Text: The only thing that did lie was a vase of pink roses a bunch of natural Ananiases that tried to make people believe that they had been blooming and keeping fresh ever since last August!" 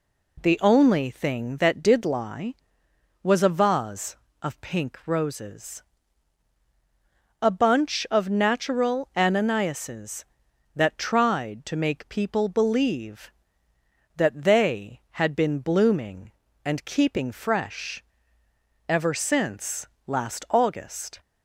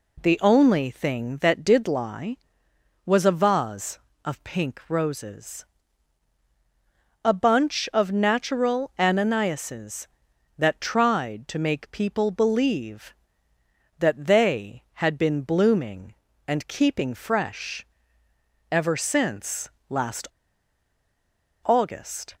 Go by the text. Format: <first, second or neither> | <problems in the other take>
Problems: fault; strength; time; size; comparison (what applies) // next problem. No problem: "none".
first | pauses between "roses" and "a"; strong; at 5.6 s; 1.6 s long; strong in the first // pauses between "fresh" and "ever"; noticeable; at 17.8 s; 0.86 s long; noticeable in the first // pauses between "since" and "last"; slight; at 19.6 s; 0.20 s long; slight in the first // pauses between "last" and "August"; strong; at 20.2 s; 1.3 s long